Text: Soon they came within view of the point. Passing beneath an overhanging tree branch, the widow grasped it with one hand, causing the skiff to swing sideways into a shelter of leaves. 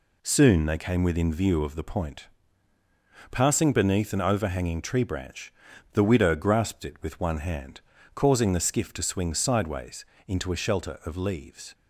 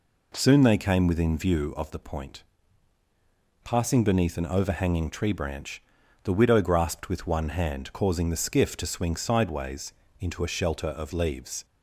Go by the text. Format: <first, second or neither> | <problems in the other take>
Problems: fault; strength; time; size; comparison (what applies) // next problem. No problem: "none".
first | skips "it"; at 7.0 s // pauses between "sideways" and "into"; slight; at 9.9 s; 0.26 s long; slight in the first